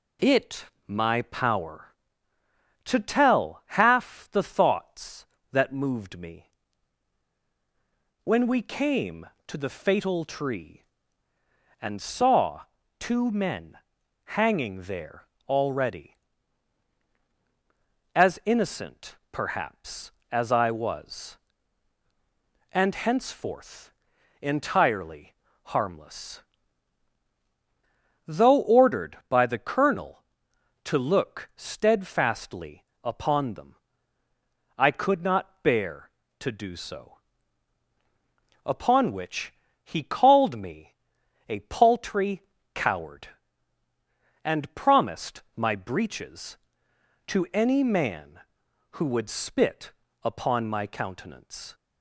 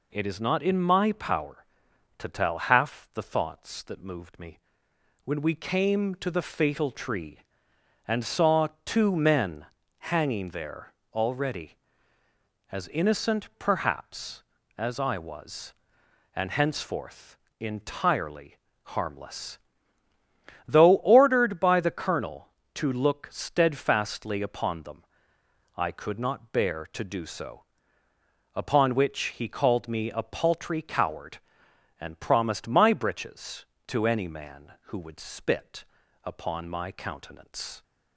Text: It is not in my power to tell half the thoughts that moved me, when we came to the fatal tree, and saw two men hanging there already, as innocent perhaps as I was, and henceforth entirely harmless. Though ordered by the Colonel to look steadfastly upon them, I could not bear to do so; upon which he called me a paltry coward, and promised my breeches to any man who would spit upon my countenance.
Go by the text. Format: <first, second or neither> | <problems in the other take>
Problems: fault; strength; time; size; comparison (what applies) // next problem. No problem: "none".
second | skips "is not in"; at 0.7 s // pauses between "saw" and "two"; at 12.6 s; 0.38 s long; slight in the second // pauses between "men" and "hanging"; noticeable; at 13.7 s; 0.60 s long; slight in the second // pauses between "there" and "already"; slight; at 15.2 s; 0.24 s long; slight in the second // pauses between "innocent" and "perhaps"; slight; at 19.1 s; 0.16 s long // pauses between "henceforth" and "entirely"; noticeable; at 23.9 s; 0.52 s long; slight in the second // pauses between "entirely" and "harmless"; slight; at 25.3 s; 0.32 s long; slight in the second // pauses between "steadfastly" and "upon"; slight; at 32.8 s; 0.18 s long // pauses between "which" and "he"; slight; at 39.5 s; 0.30 s long // pauses between "me" and "a"; noticeable; at 40.9 s; 0.54 s long // pauses between "paltry" and "coward"; slight; at 42.4 s; 0.30 s long // pauses between "spit" and "upon"; slight; at 49.9 s; 0.32 s long; also in the second